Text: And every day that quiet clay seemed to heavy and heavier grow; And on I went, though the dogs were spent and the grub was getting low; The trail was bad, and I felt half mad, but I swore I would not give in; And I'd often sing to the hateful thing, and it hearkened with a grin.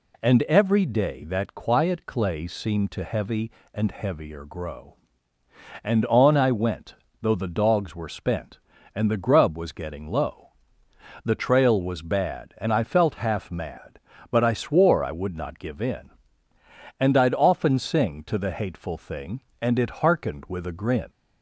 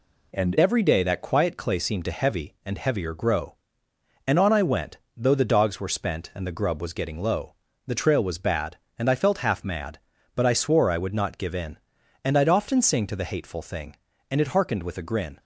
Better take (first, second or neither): first